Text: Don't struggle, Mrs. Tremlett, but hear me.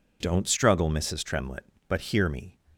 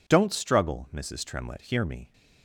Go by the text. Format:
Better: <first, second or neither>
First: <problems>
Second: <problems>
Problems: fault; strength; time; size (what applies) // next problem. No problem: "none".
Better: first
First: none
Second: skips "but"; at 1.6 s